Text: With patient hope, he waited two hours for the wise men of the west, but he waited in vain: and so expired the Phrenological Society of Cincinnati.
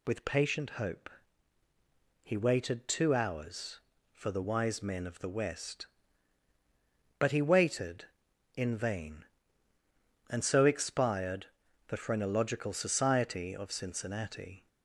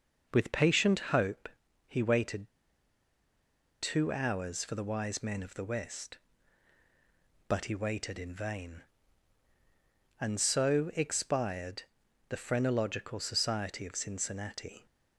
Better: first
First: pauses between "expired" and "the"; at 11.4 s; 0.42 s long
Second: pauses between "waited" and "two"; strong; at 2.4 s; 1.3 s long // pauses between "expired" and "the"; noticeable; at 11.8 s; 0.48 s long

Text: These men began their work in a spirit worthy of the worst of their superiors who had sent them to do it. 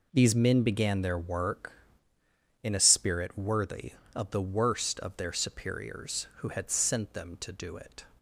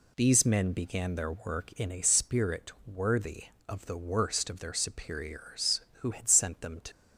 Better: first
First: none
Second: pauses between "spirit" and "worthy"; slight; at 2.6 s; 0.16 s long // stops before "do it"; at 6.9 s

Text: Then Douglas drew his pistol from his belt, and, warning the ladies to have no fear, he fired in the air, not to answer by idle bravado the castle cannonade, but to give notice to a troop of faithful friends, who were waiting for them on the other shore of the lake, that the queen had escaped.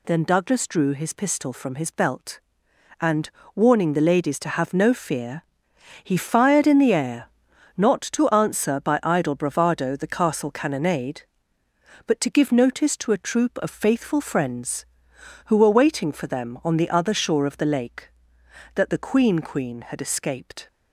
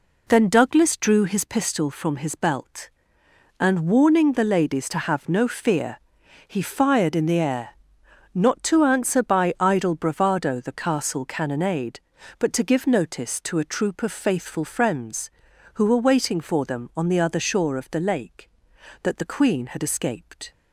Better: second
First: says "queen" twice; at 19.3 s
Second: none

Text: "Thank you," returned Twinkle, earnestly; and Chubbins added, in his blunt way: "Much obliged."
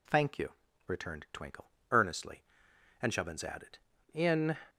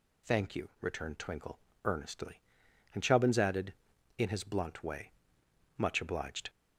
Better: second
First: stops before "his blunt way Much obliged"; at 4.6 s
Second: none

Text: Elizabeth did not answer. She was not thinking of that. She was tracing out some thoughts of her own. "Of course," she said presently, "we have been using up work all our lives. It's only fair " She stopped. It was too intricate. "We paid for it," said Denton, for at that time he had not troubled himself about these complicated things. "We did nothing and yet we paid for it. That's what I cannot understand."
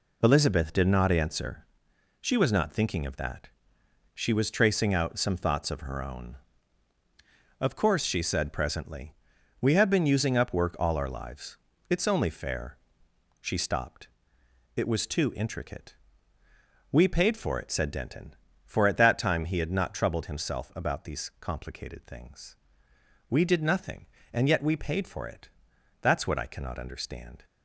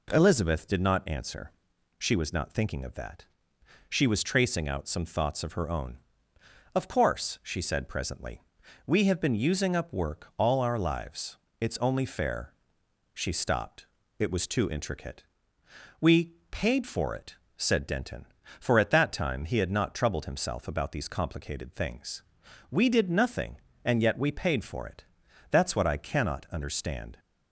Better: neither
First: none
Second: none

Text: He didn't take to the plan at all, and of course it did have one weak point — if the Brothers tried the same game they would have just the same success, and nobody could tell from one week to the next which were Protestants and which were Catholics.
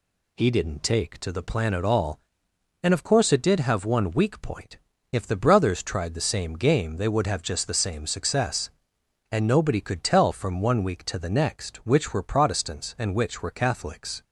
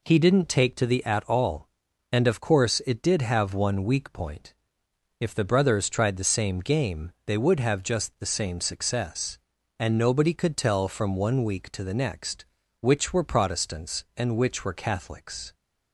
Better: first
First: none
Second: skips "plan"; at 1.0 s

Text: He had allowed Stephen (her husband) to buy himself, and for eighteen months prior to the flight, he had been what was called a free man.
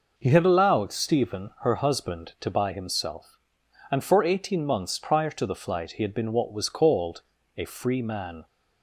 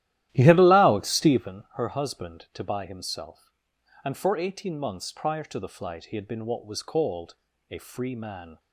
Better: first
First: pauses between "called" and "a"; slight; at 7.2 s; 0.36 s long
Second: starts louder than the rest; strong; until 1.5 s; 13.5 dB // pauses between "called" and "a"; slight; at 7.3 s; 0.36 s long

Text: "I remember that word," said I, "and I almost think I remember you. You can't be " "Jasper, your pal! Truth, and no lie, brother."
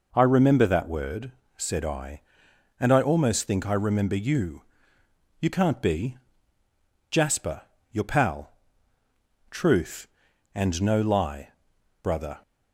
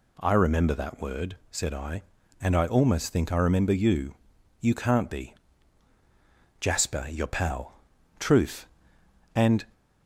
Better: first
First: none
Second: stops before "no lie brother"; at 9.7 s

